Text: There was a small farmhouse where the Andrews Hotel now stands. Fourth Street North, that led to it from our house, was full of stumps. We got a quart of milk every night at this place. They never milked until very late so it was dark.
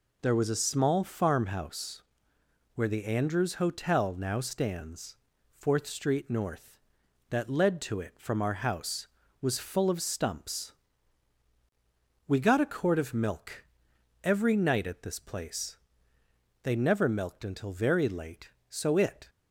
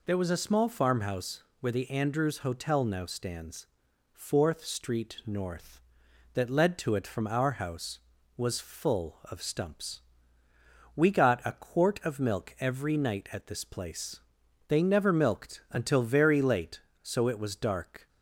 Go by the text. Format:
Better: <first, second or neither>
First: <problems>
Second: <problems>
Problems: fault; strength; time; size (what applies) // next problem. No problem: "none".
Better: second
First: pauses between "farmhouse" and "where"; noticeable; at 2.0 s; 0.74 s long // pauses between "milk" and "every"; noticeable; at 13.6 s; 0.58 s long // stops before "was dark"; at 19.2 s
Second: pauses between "farmhouse" and "where"; slight; at 1.4 s; 0.16 s long